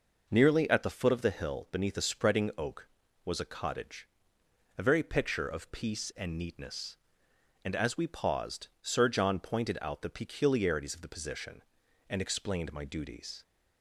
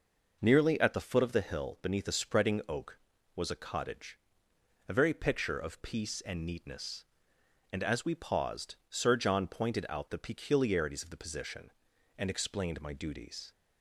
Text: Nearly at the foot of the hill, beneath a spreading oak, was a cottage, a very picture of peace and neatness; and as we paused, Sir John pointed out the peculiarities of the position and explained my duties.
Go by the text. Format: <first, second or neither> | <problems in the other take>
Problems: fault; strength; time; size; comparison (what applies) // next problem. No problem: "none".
neither | none